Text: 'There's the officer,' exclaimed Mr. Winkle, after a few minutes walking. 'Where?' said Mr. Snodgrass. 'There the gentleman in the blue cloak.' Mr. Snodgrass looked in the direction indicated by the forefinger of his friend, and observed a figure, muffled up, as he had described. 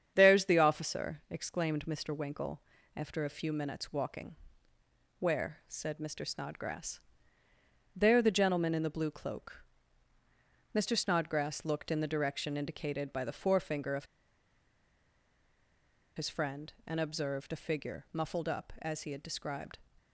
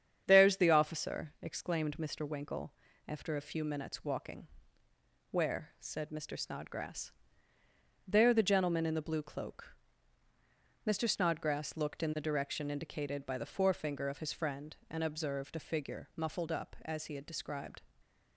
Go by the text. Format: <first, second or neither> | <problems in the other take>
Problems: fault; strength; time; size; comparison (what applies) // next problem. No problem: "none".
second | starts louder than the rest; strong; until 1.1 s; 8.5 dB; strong in the second // pauses between "of" and "his"; strong; at 14.0 s; 2.1 s long